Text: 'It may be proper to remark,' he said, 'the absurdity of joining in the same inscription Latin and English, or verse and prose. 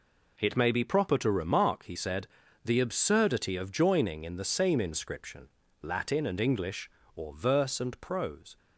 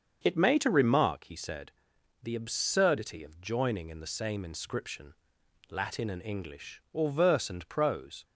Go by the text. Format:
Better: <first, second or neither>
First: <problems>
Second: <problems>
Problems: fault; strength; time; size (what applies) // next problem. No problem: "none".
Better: first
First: pauses between "inscription" and "Latin"; slight; at 5.4 s; 0.32 s long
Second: starts louder than the rest; until 1.2 s; 7 dB // skips "be proper"; at 0.5 s // pauses between "inscription" and "Latin"; noticeable; at 5.1 s; 0.54 s long